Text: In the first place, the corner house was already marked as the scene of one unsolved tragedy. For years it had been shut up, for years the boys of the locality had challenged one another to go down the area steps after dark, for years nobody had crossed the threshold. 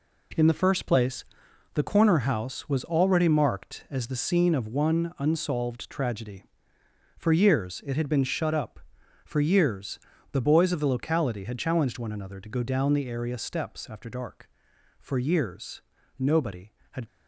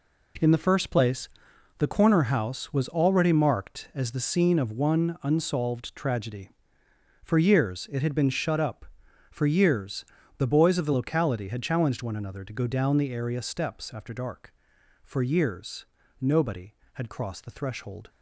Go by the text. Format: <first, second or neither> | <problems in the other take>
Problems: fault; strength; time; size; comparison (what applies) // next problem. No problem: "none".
second | pauses between "years" and "the"; slight; at 9.9 s; 0.32 s long; slight in the second // pauses between "years" and "nobody"; slight; at 15.8 s; 0.36 s long; slight in the second // stops before "crossed the threshold"; at 17.0 s